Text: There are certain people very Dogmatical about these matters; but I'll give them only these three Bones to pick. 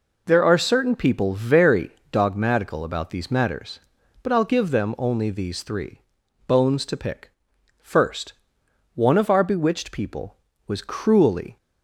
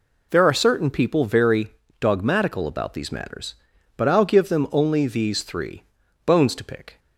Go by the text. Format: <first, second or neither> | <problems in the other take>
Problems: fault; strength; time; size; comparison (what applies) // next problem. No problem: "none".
second | pauses between "very" and "Dogmatical"; slight; at 1.9 s; 0.22 s long; slight in the second // pauses between "three" and "Bones"; at 6.0 s; 0.44 s long; also in the second // goes on to say "First One of our bewitched people was cruelly"; strong; from 7.7 s on; 3.7 s long